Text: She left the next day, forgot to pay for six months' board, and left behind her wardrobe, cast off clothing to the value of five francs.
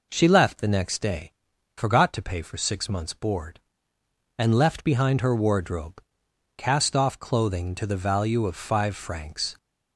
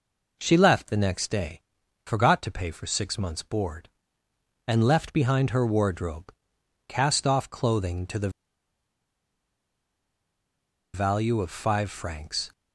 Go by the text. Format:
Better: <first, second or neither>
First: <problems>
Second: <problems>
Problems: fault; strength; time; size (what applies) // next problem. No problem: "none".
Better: first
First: none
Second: pauses between "the" and "value"; strong; at 8.2 s; 2.6 s long